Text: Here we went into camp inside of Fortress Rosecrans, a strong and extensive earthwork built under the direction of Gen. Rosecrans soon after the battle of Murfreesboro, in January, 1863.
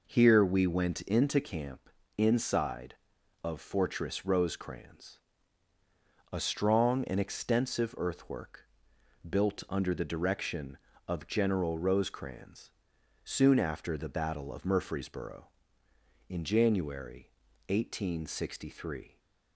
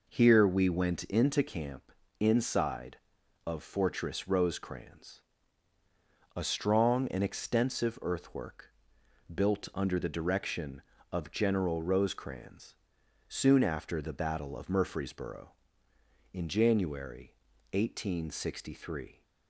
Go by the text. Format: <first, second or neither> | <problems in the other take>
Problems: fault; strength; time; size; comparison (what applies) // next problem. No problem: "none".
neither | pauses between "camp" and "inside"; slight; the same in both // pauses between "earthwork" and "built"; noticeable; the same in both // pauses between "Rosecrans" and "soon"; noticeable; the same in both